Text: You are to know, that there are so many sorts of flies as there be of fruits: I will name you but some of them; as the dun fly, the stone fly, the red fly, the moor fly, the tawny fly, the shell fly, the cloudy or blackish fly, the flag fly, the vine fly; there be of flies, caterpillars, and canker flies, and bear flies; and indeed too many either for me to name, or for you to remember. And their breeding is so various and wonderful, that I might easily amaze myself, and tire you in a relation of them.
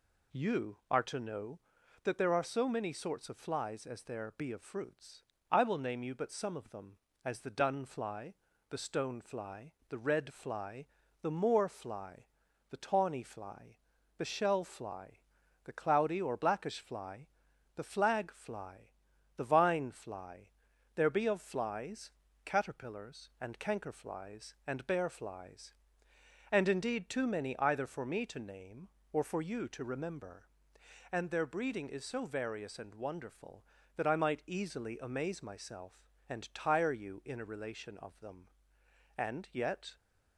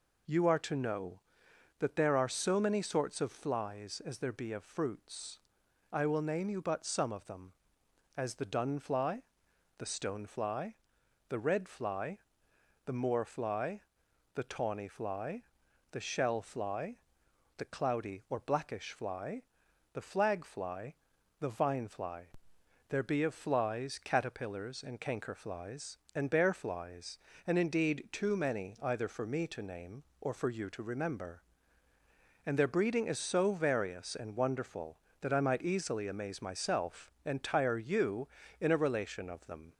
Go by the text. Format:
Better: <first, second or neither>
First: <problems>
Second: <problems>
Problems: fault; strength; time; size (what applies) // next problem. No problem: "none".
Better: second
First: goes on to say "And yet"; noticeable; from 39.1 s on; 0.78 s long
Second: none